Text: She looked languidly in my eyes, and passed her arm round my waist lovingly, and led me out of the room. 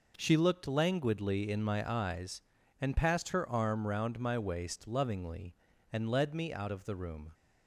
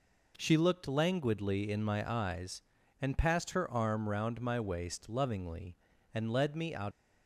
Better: first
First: none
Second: stops before "of the room"; at 6.9 s

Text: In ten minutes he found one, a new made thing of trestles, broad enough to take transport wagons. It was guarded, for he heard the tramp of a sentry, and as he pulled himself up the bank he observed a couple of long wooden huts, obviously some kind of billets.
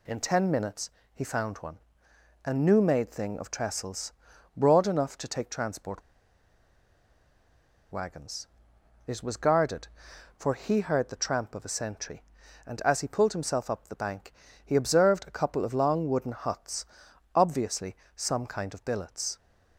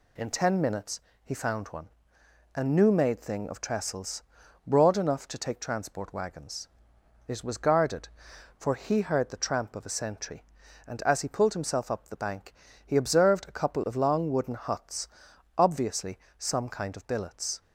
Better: second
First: pauses between "minutes" and "he"; slight; at 0.9 s; 0.22 s long // pauses between "transport" and "wagons"; strong; at 6.0 s; 1.9 s long // pauses between "bank" and "he"; slight; at 14.3 s; 0.30 s long // pauses between "obviously" and "some"; slight; at 17.9 s; 0.18 s long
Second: pauses between "minutes" and "he"; slight; at 1.0 s; 0.22 s long // pauses between "bank" and "he"; slight; at 12.5 s; 0.30 s long // pauses between "obviously" and "some"; slight; at 16.1 s; 0.18 s long

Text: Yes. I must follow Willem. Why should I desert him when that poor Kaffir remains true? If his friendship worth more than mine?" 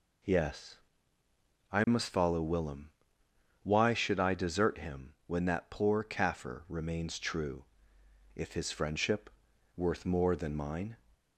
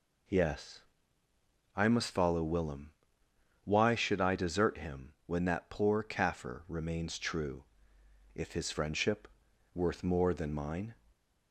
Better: neither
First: pauses between "him" and "when"; slight; at 5.0 s; 0.16 s long // pauses between "friendship" and "worth"; noticeable; at 9.2 s; 0.46 s long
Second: pauses between "him" and "when"; slight; at 5.0 s; 0.16 s long // pauses between "friendship" and "worth"; noticeable; at 9.2 s; 0.46 s long

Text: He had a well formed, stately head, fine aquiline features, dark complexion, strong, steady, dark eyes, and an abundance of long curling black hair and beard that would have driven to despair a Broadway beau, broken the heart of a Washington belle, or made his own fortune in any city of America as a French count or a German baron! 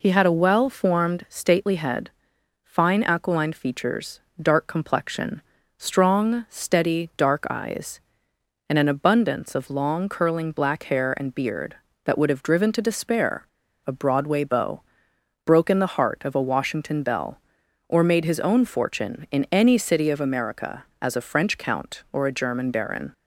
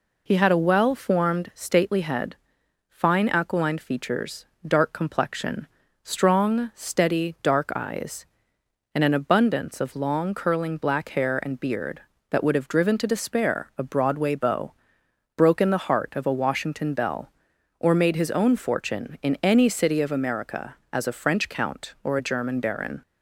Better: second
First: pauses between "despair" and "a"; at 13.4 s; 0.41 s long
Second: none

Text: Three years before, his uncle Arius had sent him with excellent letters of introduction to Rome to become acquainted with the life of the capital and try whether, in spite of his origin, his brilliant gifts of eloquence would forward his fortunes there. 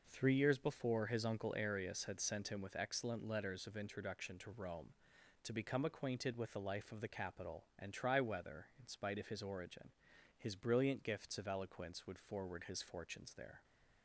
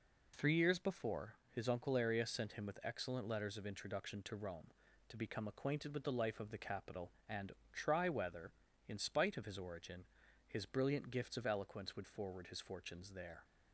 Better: first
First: none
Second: skips "had"; at 2.2 s // pauses between "and" and "try"; slight; at 7.5 s; 0.20 s long

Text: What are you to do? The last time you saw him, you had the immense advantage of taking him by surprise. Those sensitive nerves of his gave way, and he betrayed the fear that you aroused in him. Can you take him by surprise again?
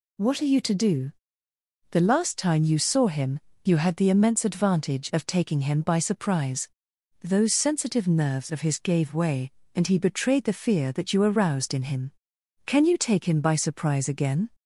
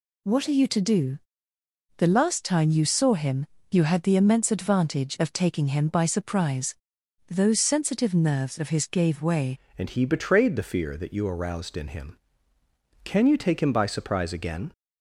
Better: first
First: none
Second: changes voice at "and"; from 9.7 s on; 5.0 s long

